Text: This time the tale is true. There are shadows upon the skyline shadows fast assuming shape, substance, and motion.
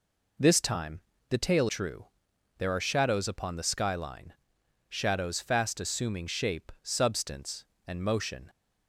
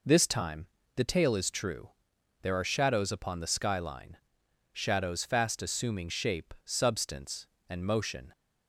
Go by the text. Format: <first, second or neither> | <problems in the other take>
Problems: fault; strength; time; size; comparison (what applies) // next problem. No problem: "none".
second | pauses between "time" and "the"; slight; at 0.9 s; 0.30 s long; slight in the second // skips "is"; at 1.6 s // pauses between "skyline" and "shadows"; noticeable; at 4.3 s; 0.56 s long; noticeable in the second